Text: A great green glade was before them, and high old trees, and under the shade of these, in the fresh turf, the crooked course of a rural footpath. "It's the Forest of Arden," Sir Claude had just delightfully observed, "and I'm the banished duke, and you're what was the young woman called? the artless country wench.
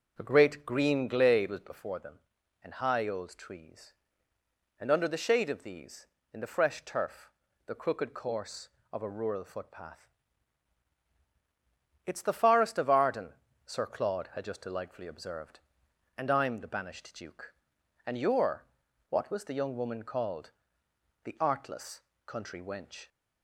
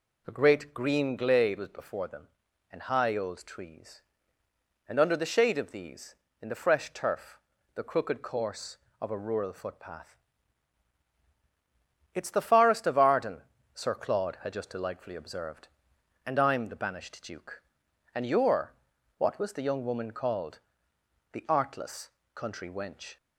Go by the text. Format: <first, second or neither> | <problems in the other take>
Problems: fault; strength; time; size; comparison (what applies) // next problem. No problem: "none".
second | starts louder than the rest; noticeable; until 1.7 s; 6 dB // pauses between "you're" and "what"; noticeable; at 18.6 s; 0.46 s long; noticeable in the second // pauses between "artless" and "country"; slight; at 22.0 s; 0.24 s long; slight in the second